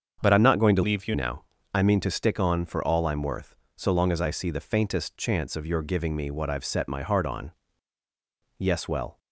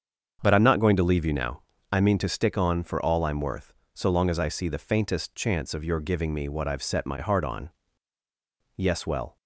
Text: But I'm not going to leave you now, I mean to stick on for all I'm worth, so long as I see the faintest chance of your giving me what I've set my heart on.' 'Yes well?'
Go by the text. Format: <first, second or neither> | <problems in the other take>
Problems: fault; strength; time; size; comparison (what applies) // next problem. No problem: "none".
second | starts louder than the rest; strong; until 1.2 s; 7 dB; strong in the second // changes voice from "leave" to "you"; from 0.8 to 1.1 s; 0.3 s long